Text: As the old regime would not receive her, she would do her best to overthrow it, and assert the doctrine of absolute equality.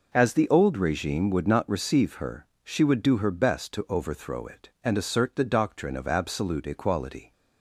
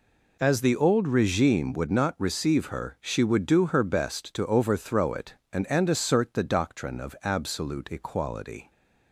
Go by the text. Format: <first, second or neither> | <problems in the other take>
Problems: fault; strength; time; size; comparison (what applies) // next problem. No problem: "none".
first | says "and" twice; at 5.6 s